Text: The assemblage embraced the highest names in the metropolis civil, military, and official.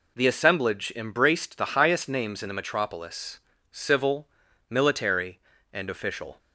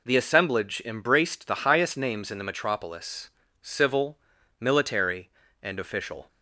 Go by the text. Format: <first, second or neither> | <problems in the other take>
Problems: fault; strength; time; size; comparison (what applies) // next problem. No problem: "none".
neither | pauses between "metropolis" and "civil"; slight; the same in both